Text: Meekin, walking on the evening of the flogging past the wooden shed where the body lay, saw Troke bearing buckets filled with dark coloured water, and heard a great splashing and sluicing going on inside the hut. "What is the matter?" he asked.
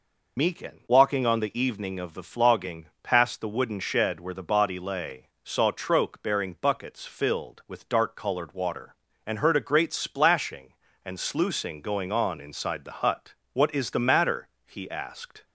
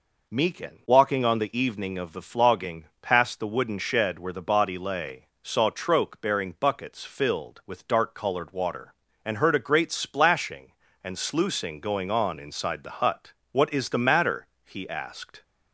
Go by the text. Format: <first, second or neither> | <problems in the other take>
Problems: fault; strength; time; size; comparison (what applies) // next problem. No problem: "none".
second | loses the start of "Meekin"; at 0.3 s; 75 ms